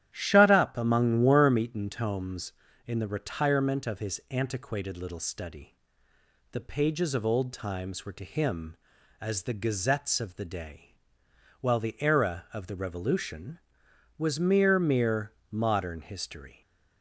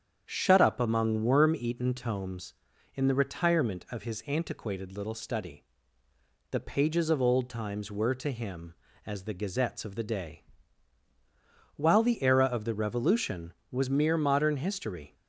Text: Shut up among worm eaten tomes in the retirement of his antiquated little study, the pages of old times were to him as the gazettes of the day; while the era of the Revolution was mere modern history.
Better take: second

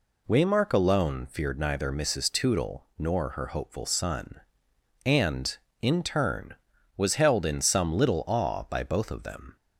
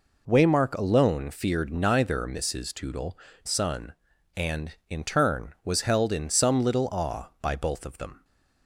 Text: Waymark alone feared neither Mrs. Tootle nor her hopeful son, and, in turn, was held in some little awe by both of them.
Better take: first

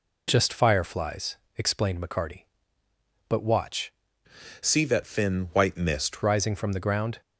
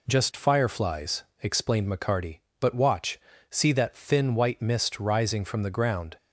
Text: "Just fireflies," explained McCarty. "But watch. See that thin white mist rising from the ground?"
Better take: second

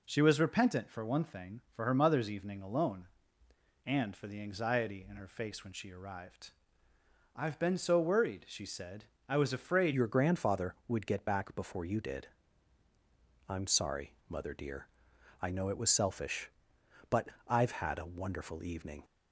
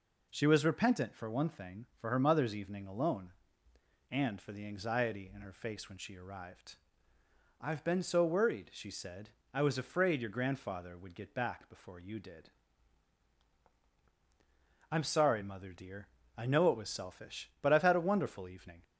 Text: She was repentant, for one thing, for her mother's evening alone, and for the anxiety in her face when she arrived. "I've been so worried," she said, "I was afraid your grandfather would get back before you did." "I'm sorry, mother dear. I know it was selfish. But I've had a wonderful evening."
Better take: second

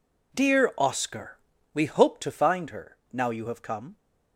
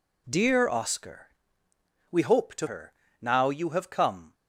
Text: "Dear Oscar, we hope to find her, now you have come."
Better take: first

